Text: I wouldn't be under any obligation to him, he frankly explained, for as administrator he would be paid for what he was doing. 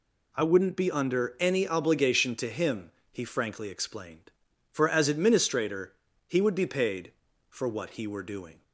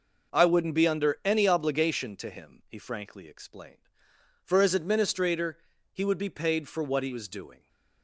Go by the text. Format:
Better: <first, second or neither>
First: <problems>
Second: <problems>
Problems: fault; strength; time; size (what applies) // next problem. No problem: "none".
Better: second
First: pauses between "administrator" and "he"; slight; at 5.9 s; 0.34 s long // says "were" for "was"; at 8.0 s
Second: pauses between "administrator" and "he"; slight; at 5.5 s; 0.34 s long